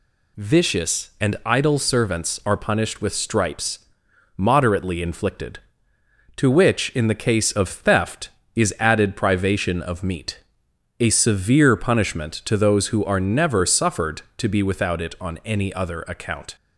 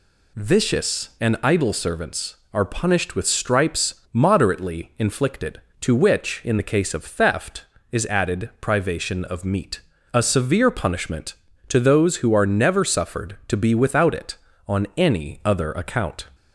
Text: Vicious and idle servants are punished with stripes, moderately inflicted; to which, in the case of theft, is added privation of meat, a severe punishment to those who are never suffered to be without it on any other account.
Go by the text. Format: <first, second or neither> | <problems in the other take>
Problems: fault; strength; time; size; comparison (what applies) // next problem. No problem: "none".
neither | none